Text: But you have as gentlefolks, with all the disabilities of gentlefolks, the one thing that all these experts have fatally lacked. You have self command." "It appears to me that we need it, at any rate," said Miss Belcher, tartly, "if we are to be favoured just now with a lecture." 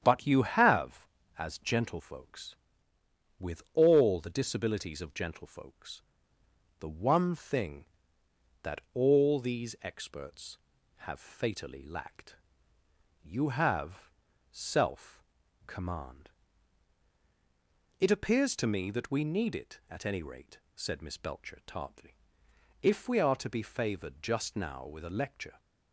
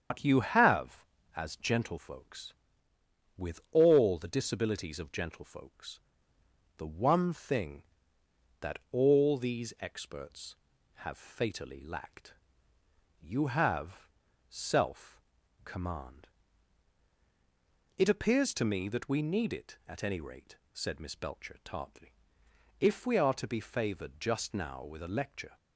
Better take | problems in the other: first | loses the start of "But"; at 0.1 s; 95 ms // starts louder than the rest; strong; until 1.4 s; 7.5 dB; strong in the first // pauses between "have" and "self"; at 14.0 s; 0.40 s long; also in the first // pauses between "self" and "command"; at 15.2 s; 0.44 s long; also in the first

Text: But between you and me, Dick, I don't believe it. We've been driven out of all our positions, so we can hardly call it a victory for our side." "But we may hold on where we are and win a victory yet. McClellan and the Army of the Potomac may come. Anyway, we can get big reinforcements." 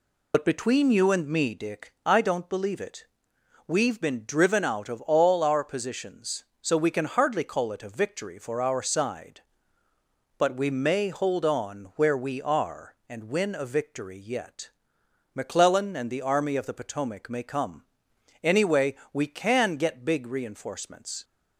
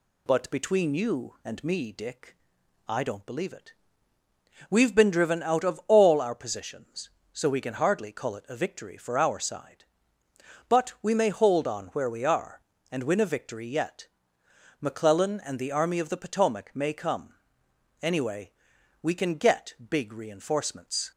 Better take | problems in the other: second | loses the start of "But"; at 0.3 s; 65 ms

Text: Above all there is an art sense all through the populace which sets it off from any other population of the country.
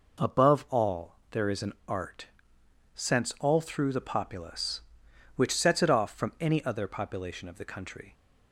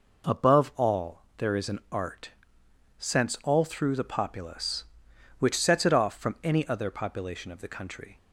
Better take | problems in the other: neither | pauses between "all" and "there"; slight; the same in both // pauses between "art" and "sense"; noticeable; the same in both

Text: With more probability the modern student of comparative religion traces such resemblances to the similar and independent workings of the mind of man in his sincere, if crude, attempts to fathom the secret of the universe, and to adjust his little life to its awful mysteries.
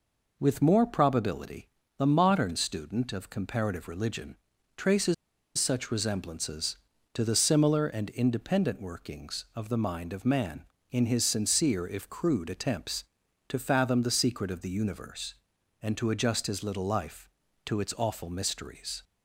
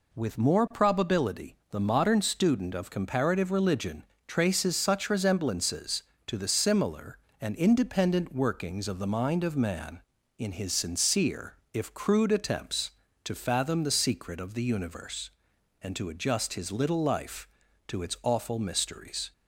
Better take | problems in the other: second | pauses between "probability" and "the"; slight; at 1.6 s; 0.30 s long // pauses between "religion" and "traces"; at 4.3 s; 0.40 s long; slight in the second // pauses between "traces" and "such"; at 5.1 s; 0.43 s long

